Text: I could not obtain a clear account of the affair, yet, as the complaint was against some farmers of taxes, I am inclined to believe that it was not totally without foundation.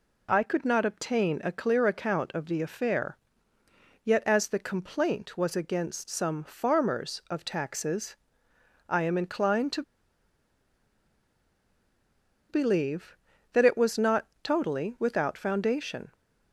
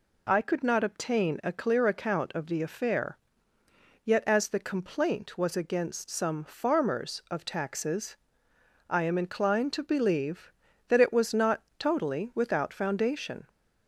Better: second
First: pauses between "to" and "believe"; strong; at 9.8 s; 2.6 s long // pauses between "not" and "totally"; slight; at 14.2 s; 0.16 s long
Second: pauses between "not" and "totally"; slight; at 11.6 s; 0.16 s long

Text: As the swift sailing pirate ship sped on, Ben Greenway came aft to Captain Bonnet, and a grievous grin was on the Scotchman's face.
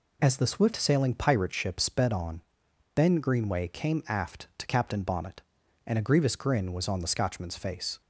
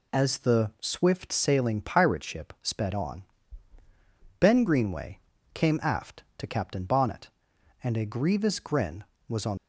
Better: first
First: none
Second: pauses between "Greenway" and "came"; slight; at 5.1 s; 0.32 s long // stops before "the Scotchman's face"; at 9.5 s

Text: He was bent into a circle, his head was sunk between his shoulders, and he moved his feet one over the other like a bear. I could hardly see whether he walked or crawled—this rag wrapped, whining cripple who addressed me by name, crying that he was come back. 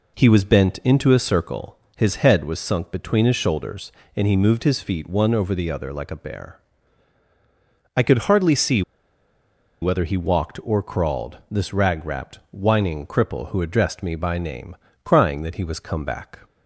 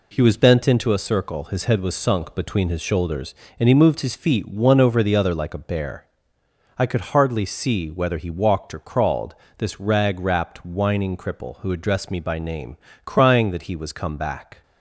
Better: second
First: pauses between "see" and "whether"; at 8.8 s; 1.0 s long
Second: none

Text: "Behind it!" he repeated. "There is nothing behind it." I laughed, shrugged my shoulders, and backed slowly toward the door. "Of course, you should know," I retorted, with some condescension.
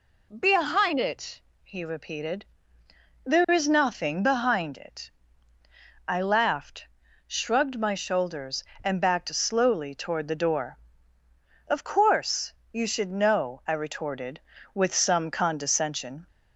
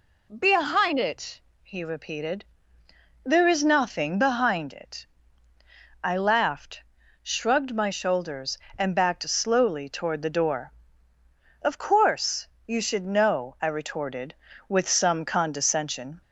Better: neither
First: none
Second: none

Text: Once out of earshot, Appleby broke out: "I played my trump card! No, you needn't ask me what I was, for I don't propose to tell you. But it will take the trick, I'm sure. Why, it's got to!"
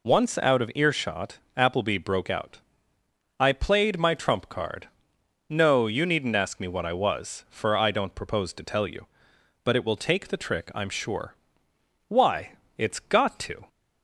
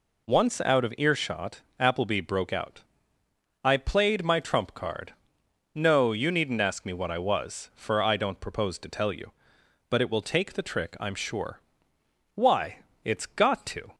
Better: neither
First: none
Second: none

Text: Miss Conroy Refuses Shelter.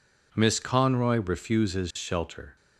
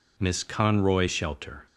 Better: first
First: none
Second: skips "Refuses"; at 1.0 s

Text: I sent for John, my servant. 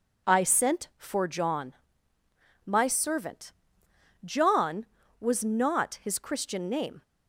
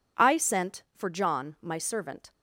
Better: second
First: goes on to say "John was not his Christian name"; strong; from 4.2 s on; 2.7 s long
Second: none

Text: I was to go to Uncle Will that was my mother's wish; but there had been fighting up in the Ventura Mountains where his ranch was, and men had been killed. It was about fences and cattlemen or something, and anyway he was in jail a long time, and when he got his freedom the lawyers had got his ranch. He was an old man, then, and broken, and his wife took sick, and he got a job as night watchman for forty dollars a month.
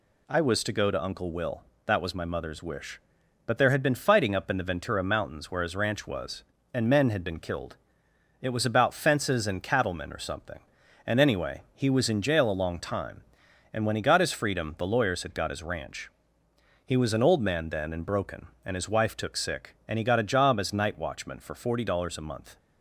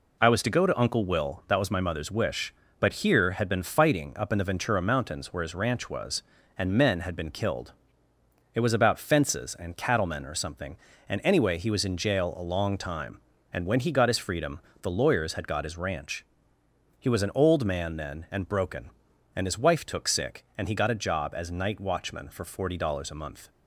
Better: first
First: none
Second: says "here" for "there"; at 3.0 s // pauses between "freedom" and "the"; slight; at 14.5 s; 0.24 s long

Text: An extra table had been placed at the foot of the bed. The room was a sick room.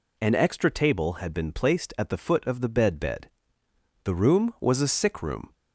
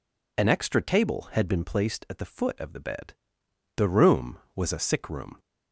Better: second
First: says "bed" twice; at 2.9 s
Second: none

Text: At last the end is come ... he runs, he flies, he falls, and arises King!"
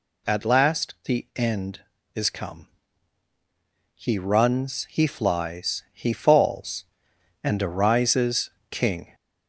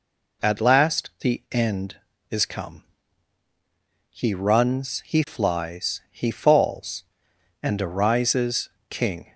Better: second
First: gets louder; slight; throughout; 2 dB // pauses between "arises" and "King"; slight; at 8.5 s; 0.20 s long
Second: pauses between "arises" and "King"; slight; at 8.6 s; 0.20 s long

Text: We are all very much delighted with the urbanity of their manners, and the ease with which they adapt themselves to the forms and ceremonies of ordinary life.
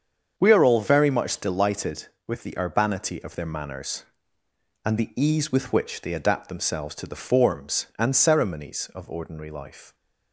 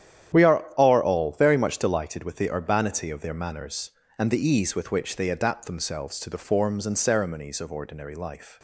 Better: first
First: starts louder than the rest; strong; until 1.3 s; 7 dB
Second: starts louder than the rest; strong; until 1.4 s; 10.5 dB // says "are" twice; at 0.7 s

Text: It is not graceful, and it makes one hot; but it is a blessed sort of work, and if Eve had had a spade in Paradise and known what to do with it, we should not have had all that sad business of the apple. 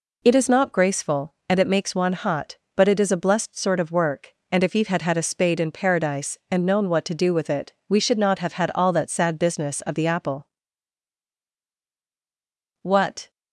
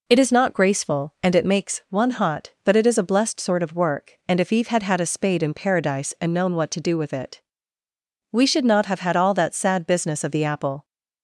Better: second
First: goes on to say "What"; slight; from 12.8 s on; 0.48 s long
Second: none

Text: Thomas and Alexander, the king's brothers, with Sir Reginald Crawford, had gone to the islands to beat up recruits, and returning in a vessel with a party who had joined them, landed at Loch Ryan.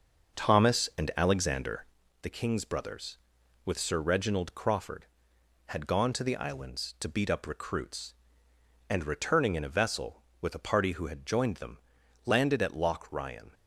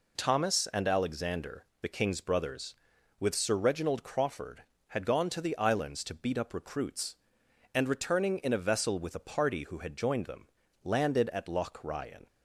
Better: second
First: starts louder than the rest; noticeable; until 1.9 s; 6 dB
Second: none

